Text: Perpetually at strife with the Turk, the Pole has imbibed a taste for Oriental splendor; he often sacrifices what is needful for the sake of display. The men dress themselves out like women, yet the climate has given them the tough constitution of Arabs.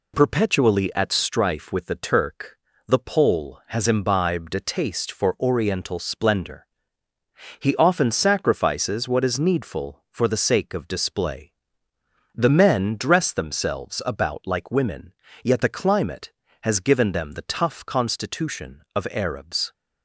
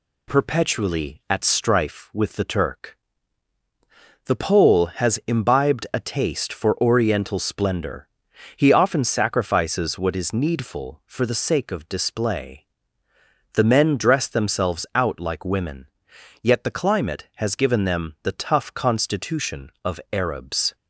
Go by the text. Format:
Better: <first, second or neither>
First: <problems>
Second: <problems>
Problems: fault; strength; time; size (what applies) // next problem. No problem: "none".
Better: second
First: says "about" for "out"; at 14.0 s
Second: none